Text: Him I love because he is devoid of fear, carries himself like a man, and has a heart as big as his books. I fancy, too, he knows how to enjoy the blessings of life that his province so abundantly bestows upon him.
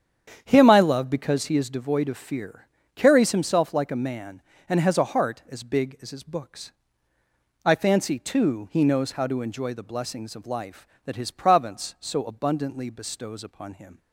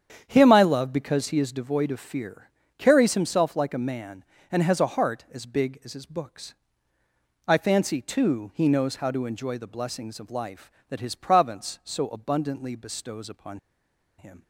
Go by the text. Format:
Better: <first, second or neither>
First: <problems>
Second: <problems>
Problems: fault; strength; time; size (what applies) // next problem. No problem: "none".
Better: first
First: starts louder than the rest; strong; until 1.4 s; 8.5 dB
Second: starts louder than the rest; strong; until 1.2 s; 8.5 dB // pauses between "upon" and "him"; noticeable; at 13.5 s; 0.59 s long